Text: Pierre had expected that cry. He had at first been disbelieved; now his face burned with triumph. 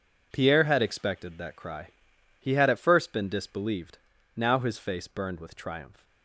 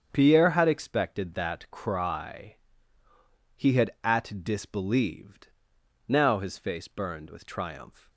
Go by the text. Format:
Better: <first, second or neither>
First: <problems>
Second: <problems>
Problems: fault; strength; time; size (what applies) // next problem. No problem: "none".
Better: first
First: none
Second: starts louder than the rest; strong; until 1.1 s; 7.5 dB // skips "first been"; at 4.4 s